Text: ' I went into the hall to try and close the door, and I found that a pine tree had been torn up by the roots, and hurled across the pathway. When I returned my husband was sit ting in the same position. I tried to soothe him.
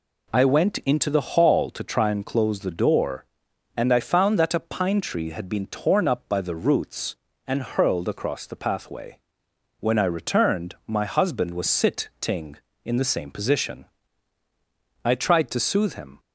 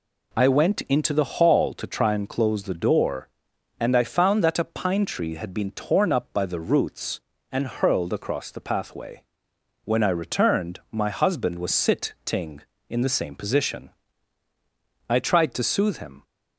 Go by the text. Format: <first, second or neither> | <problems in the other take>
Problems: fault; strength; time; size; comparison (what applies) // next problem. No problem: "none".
neither | none